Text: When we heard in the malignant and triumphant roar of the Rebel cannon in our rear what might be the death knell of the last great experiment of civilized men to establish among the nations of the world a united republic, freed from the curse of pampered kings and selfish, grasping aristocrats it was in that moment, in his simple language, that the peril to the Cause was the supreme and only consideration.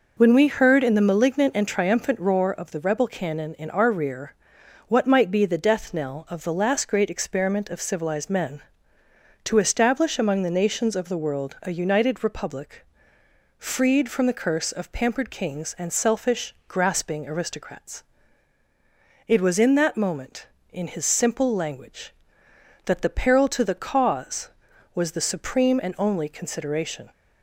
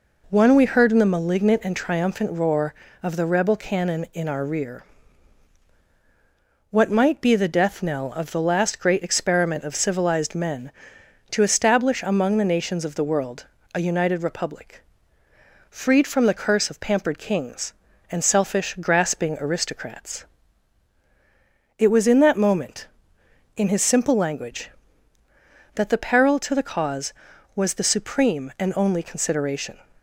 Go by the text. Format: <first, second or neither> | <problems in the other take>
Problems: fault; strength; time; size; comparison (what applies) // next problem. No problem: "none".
first | says "One" for "When"; at 0.3 s // pauses between "rear" and "what"; strong; at 4.8 s; 1.8 s long; noticeable in the first // pauses between "world" and "a"; slight; at 13.4 s; 0.28 s long // pauses between "aristocrats" and "it"; strong; at 20.2 s; 1.5 s long; strong in the first